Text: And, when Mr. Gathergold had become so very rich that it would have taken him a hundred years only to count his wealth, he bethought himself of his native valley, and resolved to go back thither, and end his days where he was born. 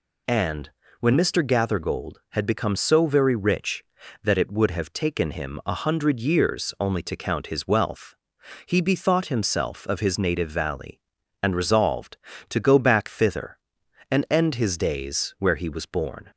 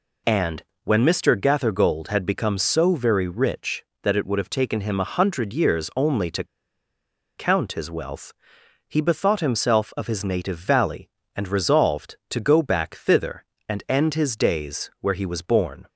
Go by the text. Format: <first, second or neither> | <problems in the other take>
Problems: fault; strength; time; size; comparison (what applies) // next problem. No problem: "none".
first | pauses between "to" and "count"; noticeable; at 6.4 s; 0.92 s long